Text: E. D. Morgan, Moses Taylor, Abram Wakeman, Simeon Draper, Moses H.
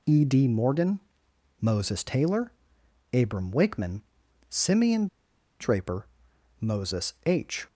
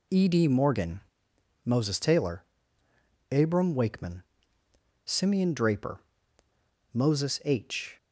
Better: second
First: pauses between "Simeon" and "Draper"; noticeable; at 5.0 s; 0.53 s long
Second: none

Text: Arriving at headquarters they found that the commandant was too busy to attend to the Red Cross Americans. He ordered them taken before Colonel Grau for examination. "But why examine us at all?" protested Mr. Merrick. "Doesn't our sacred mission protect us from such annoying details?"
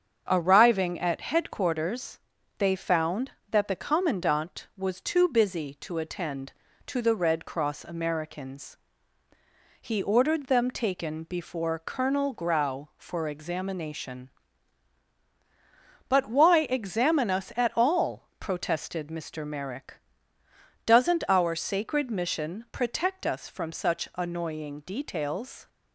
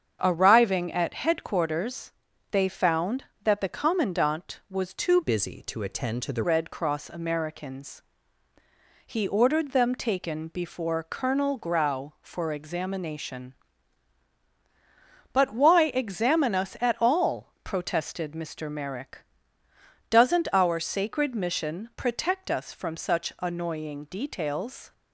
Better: first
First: starts louder than the rest; until 1.3 s; 7 dB // pauses between "headquarters" and "they"; at 2.1 s; 0.38 s long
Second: starts louder than the rest; strong; until 1.2 s; 7 dB // pauses between "headquarters" and "they"; at 2.1 s; 0.38 s long // changes voice from "busy" to "the"; from 5.2 to 6.4 s; 1.2 s long

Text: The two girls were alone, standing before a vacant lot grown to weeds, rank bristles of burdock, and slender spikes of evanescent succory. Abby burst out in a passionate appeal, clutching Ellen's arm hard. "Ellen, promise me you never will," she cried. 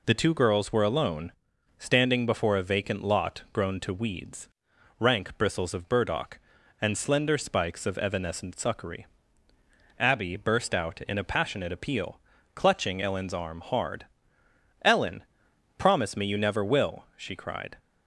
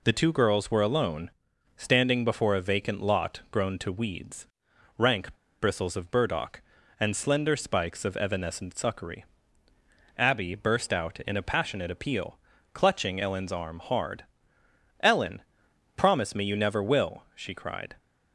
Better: first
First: none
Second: pauses between "rank" and "bristles"; slight; at 5.3 s; 0.28 s long

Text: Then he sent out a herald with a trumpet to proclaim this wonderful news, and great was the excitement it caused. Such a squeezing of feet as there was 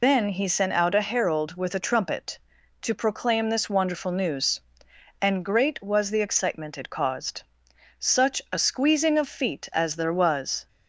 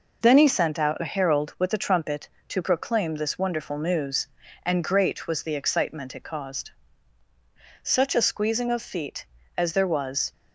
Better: second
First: loses the start of "Then"; at 0.0 s; 100 ms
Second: none

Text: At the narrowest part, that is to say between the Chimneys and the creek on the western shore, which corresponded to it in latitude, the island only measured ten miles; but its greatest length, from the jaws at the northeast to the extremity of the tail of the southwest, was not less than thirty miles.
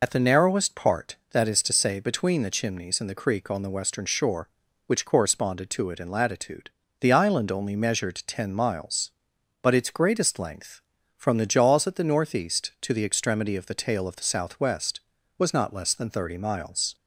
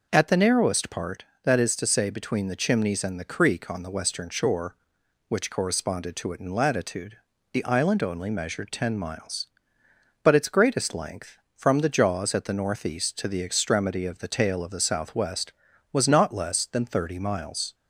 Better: second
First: loses the start of "At"; at 0.0 s; 70 ms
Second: none

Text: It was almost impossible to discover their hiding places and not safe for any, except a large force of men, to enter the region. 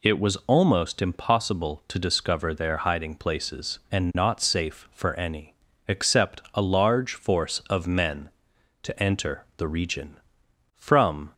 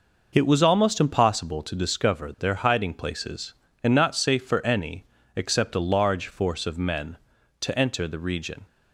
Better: second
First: goes on to say "From"; from 10.7 s on; 0.58 s long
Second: none

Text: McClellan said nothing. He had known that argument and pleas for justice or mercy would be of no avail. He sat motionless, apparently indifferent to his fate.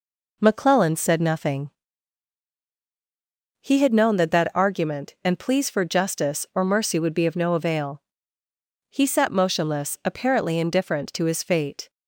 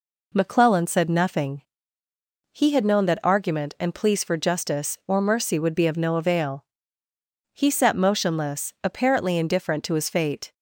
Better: second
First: says "that" twice; at 4.2 s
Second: none

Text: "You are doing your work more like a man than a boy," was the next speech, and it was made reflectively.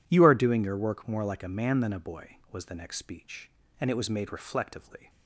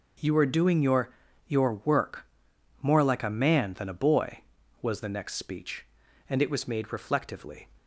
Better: first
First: none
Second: says "your" twice; at 1.4 s // pauses between "work" and "more"; noticeable; at 2.2 s; 0.56 s long

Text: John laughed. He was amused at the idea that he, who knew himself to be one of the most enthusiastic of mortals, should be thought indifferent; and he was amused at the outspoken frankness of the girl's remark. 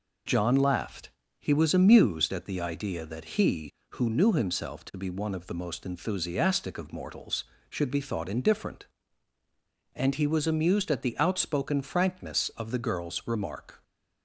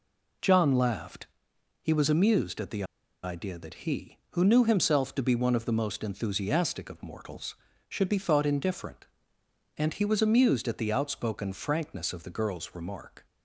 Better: first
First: none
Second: pauses between "the" and "idea"; at 2.8 s; 0.39 s long

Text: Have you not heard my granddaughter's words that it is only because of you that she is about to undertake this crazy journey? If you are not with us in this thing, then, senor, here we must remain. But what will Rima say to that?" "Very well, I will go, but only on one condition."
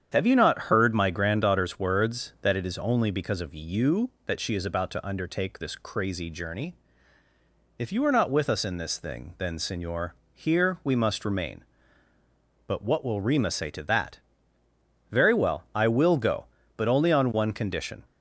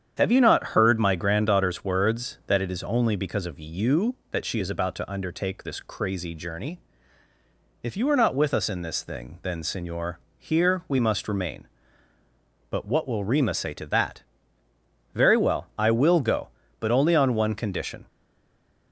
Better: first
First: starts louder than the rest; strong; until 1.1 s; 8.5 dB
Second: starts louder than the rest; strong; until 1.1 s; 8.5 dB // stays silent after the last word; slight; from 18.0 s on; 0.9 s long

